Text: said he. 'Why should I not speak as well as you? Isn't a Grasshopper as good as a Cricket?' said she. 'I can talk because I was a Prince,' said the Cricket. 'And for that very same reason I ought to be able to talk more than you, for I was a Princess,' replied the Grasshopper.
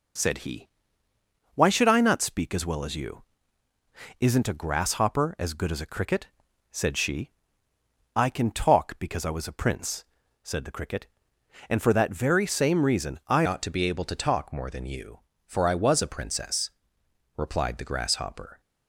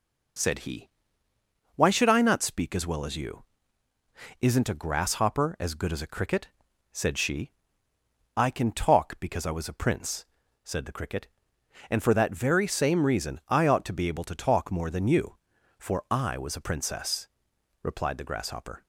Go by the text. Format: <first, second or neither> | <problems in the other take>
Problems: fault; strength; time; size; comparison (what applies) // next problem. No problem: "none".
second | changes voice at "ought"; from 13.4 s on; 5.1 s long